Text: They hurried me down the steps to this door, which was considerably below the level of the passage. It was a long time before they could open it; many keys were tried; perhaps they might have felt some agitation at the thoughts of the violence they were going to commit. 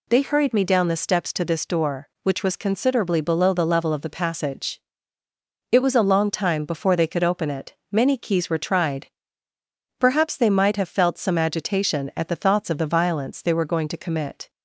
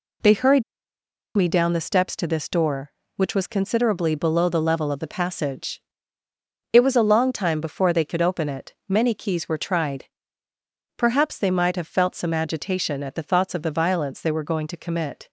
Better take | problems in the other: first | pauses between "hurried" and "me"; noticeable; at 0.6 s; 0.75 s long

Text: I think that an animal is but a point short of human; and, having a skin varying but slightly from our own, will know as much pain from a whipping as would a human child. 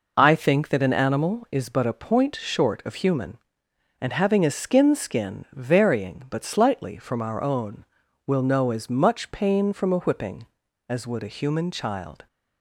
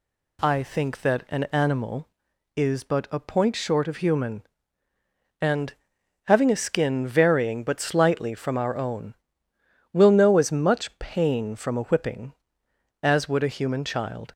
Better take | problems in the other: second | says "skin" twice; at 4.9 s

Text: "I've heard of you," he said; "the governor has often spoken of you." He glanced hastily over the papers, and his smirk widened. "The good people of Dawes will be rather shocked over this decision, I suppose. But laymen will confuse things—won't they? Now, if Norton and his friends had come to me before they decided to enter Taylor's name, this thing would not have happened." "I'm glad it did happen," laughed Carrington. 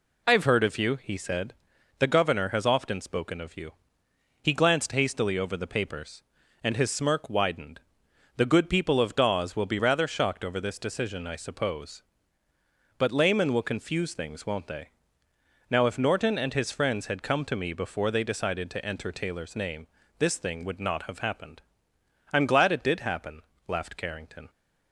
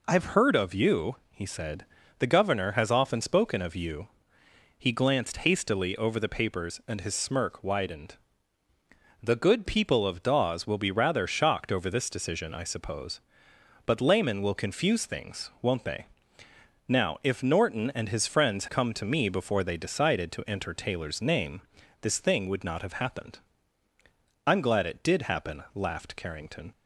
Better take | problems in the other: first | skips "had"; at 18.6 s

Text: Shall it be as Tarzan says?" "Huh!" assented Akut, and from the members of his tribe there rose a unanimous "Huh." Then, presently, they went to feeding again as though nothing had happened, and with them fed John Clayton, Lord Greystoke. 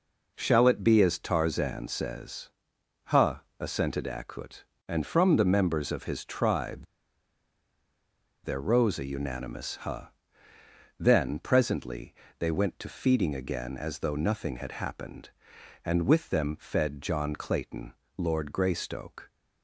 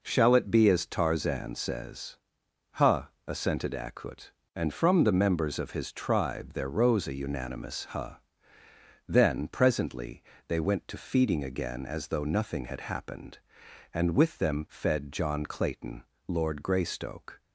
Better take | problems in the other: second | pauses between "tribe" and "there"; strong; at 6.8 s; 1.5 s long

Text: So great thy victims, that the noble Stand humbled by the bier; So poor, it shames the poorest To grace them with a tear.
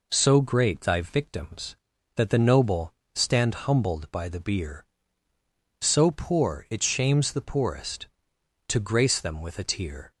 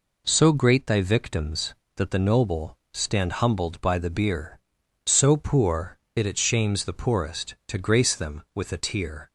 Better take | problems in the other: first | pauses between "noble" and "Stand"; slight; at 2.7 s; 0.16 s long; slight in the first // says "it" twice; at 6.2 s

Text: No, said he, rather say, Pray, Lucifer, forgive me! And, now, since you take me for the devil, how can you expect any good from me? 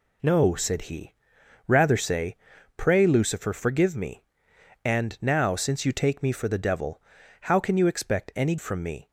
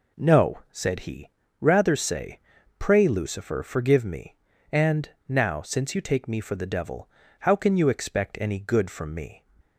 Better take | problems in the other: second | skips "good"; at 8.5 s

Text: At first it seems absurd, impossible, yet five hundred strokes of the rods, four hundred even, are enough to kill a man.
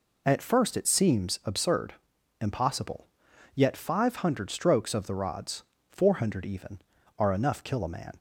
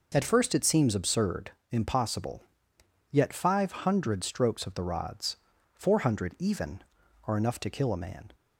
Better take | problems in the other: second | skips "to"; at 7.6 s

